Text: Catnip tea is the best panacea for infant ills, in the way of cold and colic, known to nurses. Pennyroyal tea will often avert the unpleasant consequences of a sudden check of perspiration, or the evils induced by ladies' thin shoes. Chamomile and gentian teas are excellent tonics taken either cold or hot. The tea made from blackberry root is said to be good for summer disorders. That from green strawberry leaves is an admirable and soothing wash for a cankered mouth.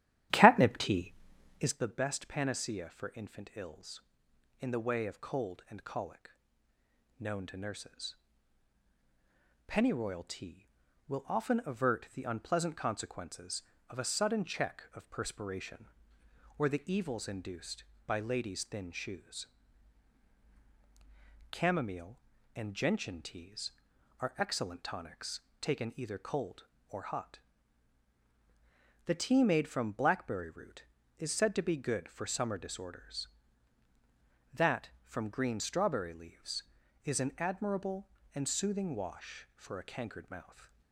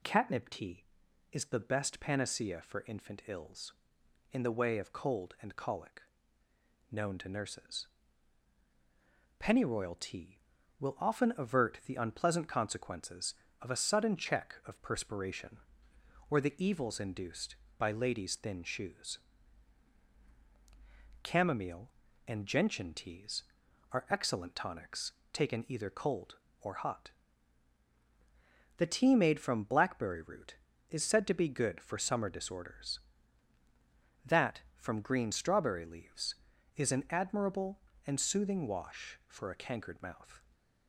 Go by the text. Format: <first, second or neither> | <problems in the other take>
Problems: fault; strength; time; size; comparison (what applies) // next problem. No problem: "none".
second | starts louder than the rest; strong; until 1.9 s; 12.5 dB // pauses between "tonics" and "taken"; slight; at 25.3 s; 0.20 s long; slight in the second // stays silent after the last word; slight; from 40.4 s on; 0.5 s long